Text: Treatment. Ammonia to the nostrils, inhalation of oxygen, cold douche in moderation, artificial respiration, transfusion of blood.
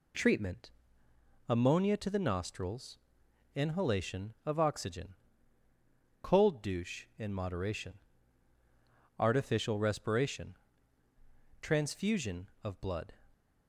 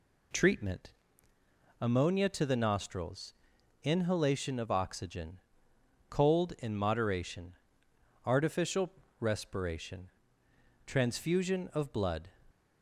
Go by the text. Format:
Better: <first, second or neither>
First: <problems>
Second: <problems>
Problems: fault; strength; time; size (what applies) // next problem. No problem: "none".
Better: first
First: none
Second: skips "douche"; at 6.5 s // pauses between "artificial" and "respiration"; slight; at 8.8 s; 0.30 s long